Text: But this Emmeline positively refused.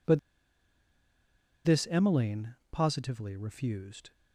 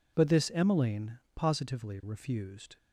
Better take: second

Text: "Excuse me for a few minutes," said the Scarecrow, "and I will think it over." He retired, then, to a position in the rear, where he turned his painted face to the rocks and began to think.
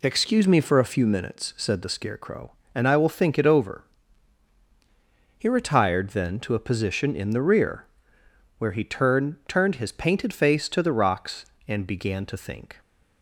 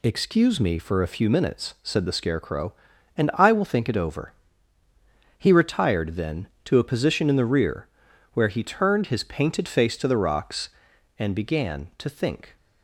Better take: second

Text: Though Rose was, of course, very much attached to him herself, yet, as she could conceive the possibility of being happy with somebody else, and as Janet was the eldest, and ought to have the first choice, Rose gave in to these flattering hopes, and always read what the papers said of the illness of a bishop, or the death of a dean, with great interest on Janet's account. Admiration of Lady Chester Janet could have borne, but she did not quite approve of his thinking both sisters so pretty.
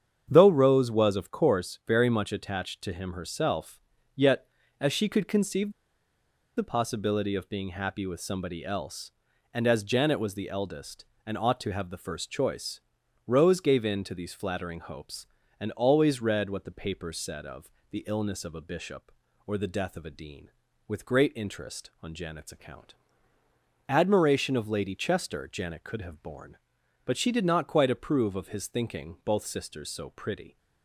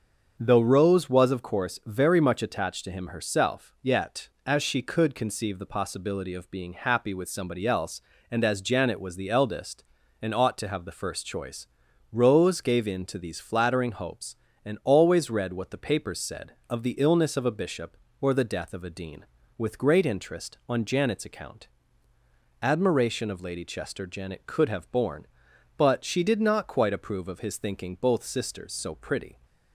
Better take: second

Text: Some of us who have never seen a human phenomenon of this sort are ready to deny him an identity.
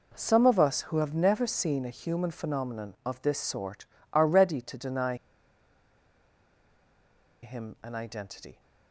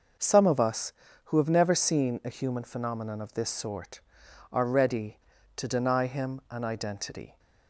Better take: second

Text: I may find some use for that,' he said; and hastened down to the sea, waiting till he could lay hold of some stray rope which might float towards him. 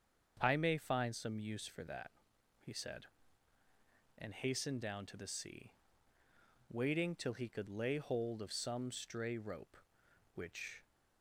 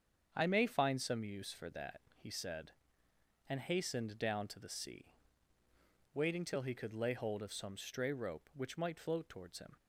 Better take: second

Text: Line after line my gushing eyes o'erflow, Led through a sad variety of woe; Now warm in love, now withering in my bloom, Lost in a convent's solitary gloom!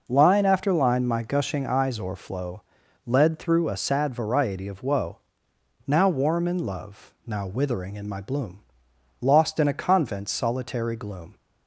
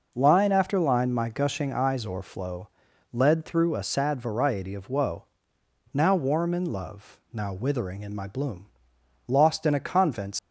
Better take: first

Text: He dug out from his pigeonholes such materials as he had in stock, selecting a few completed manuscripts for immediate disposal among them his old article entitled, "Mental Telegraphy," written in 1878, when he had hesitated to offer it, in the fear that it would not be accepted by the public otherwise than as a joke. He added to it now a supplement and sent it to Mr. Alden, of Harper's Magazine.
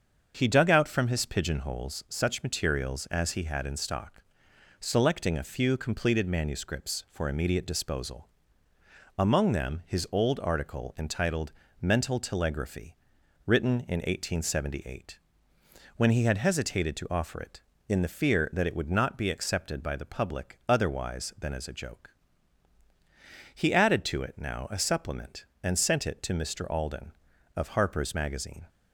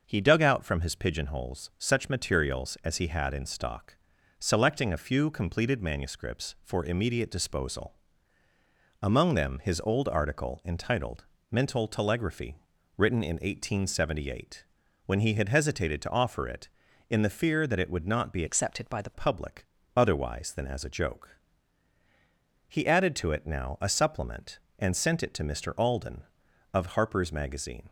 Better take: first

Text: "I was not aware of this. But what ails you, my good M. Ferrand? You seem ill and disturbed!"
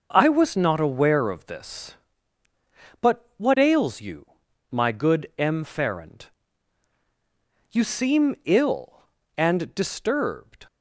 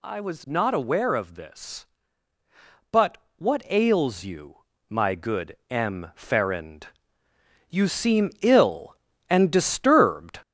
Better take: first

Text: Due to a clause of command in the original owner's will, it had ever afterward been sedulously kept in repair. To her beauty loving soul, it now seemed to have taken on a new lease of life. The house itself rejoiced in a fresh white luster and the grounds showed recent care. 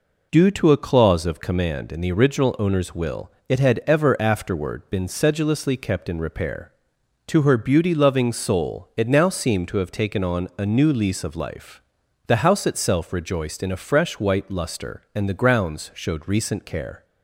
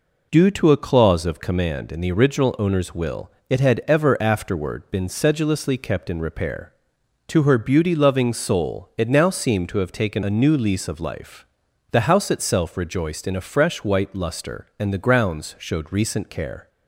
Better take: first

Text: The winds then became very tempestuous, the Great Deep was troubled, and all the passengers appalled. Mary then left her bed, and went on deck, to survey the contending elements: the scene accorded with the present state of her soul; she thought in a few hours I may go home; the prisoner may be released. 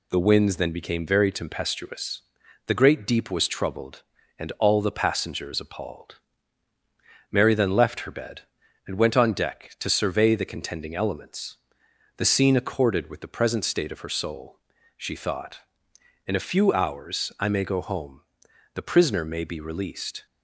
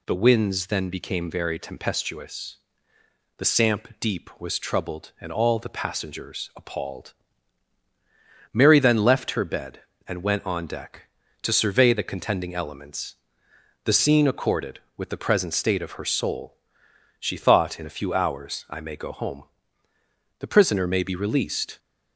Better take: first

